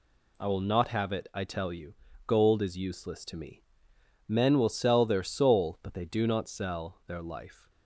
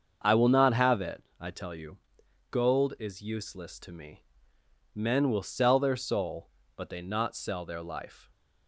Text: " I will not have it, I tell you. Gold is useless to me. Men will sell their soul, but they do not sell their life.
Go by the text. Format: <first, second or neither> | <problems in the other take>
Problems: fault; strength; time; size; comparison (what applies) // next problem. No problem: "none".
first | starts louder than the rest; until 1.4 s; 6.5 dB // skips "do"; at 7.0 s